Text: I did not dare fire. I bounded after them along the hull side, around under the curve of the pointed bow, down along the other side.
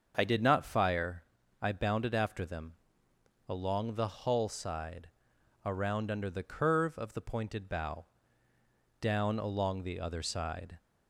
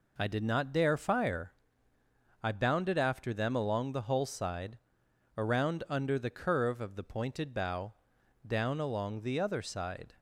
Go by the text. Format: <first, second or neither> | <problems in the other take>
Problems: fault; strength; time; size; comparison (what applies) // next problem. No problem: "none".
second | starts louder than the rest; until 1.1 s; 6.5 dB // skips "dare"; at 0.6 s // pauses between "them" and "along"; noticeable; at 2.7 s; 0.76 s long